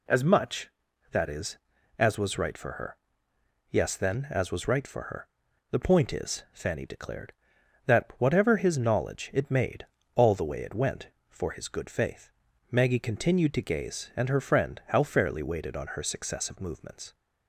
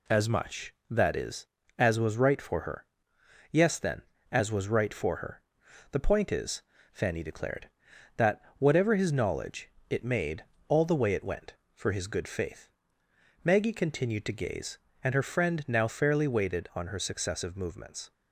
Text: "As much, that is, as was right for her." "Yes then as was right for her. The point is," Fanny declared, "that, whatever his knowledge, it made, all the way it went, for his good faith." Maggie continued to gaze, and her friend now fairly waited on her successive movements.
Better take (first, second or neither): second